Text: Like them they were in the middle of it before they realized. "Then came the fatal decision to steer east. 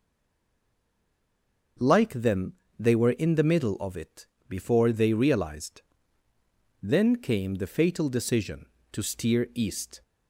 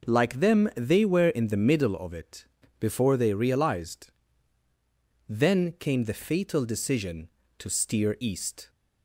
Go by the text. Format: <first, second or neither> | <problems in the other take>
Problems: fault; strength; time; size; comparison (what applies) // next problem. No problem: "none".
second | stays silent before the first word; noticeable; until 1.7 s; 1.7 s long // starts louder than the rest; until 3.0 s; 6 dB // pauses between "them" and "they"; slight; at 2.5 s; 0.26 s long // pauses between "it" and "before"; slight; at 4.2 s; 0.24 s long; slight in the second